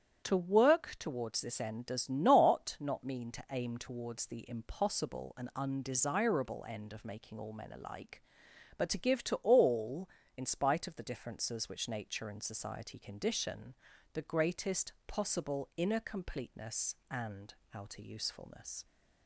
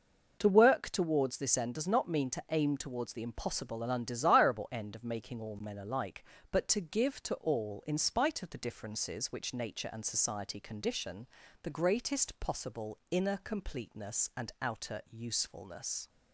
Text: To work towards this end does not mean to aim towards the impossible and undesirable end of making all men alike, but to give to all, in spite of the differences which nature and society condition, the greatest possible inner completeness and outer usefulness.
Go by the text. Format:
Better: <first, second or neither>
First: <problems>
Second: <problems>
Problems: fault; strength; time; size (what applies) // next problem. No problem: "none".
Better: second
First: starts louder than the rest; strong; until 1.2 s; 9 dB // says "not" twice; at 2.7 s // pauses between "and" and "outer"; slight; at 17.5 s; 0.18 s long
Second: none